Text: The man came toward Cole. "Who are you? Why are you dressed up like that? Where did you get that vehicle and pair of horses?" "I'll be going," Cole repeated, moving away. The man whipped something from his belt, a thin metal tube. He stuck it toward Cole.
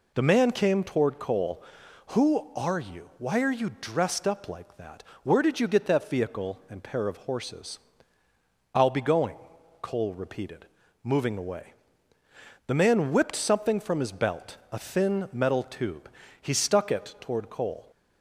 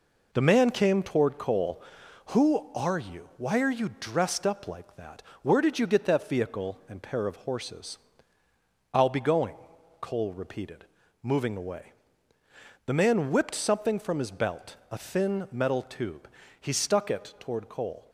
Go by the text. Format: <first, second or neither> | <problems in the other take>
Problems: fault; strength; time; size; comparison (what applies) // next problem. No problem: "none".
first | gets quieter; noticeable; throughout; 5.5 dB